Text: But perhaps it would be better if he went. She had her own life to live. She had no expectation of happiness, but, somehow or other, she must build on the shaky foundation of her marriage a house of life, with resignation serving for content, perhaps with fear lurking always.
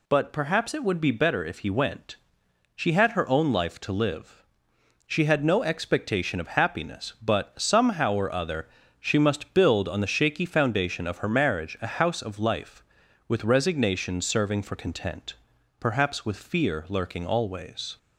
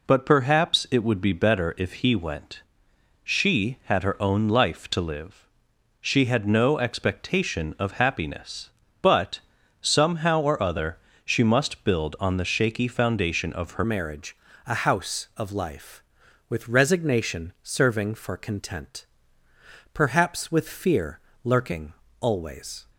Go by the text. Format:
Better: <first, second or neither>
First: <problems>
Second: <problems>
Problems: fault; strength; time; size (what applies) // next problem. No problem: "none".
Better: first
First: none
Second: changes voice at "marriage"; from 13.8 s on; 9.0 s long // pauses between "marriage" and "a"; slight; at 14.3 s; 0.30 s long // pauses between "fear" and "lurking"; slight; at 21.2 s; 0.24 s long // pauses between "lurking" and "always"; slight; at 21.9 s; 0.28 s long